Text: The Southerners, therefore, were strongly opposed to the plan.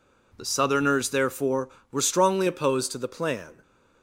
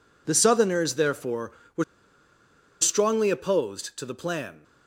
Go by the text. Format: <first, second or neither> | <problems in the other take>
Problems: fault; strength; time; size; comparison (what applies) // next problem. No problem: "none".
first | pauses between "were" and "strongly"; noticeable; at 1.8 s; 0.96 s long